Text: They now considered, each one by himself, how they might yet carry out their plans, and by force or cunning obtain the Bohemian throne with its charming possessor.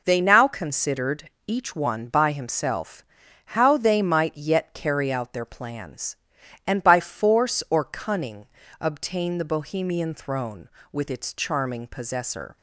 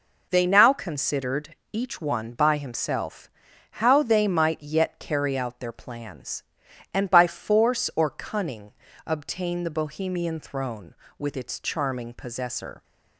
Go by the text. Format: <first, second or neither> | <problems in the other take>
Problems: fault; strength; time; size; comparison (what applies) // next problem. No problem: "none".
neither | pauses between "cunning" and "obtain"; slight; the same in both